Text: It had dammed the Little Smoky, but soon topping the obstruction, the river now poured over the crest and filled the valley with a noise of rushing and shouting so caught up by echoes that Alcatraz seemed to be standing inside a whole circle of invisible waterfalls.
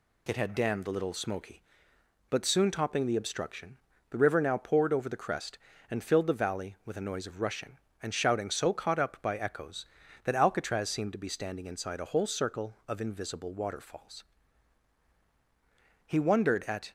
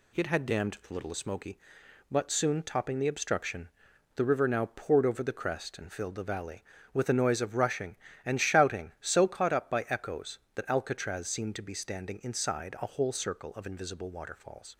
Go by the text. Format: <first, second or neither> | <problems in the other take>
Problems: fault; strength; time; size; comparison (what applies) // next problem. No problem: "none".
second | goes on to say "He wondered at"; noticeable; from 16.0 s on; 0.86 s long